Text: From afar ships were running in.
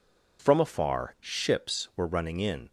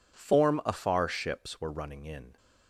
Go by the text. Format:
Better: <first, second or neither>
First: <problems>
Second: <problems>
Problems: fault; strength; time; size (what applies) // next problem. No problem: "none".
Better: first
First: none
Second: says "Form" for "From"; at 0.1 s